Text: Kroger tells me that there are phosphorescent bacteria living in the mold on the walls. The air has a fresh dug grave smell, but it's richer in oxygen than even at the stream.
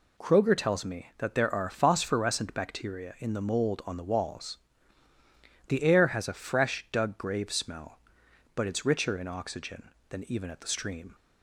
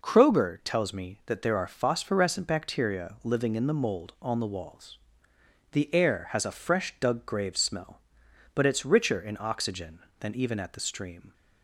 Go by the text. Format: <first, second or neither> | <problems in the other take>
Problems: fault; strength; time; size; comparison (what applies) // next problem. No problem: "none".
second | skips "living"; at 3.1 s